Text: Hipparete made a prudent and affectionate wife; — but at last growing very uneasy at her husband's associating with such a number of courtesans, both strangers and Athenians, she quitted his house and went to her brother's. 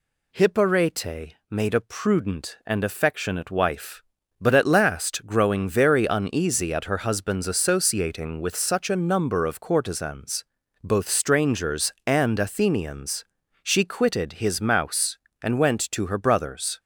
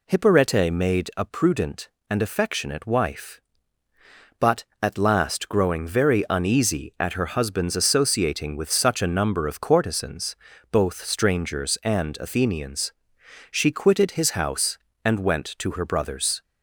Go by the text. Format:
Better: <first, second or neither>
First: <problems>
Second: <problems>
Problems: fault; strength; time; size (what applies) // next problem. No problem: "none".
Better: second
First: says "mouse" for "house"; at 14.6 s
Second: none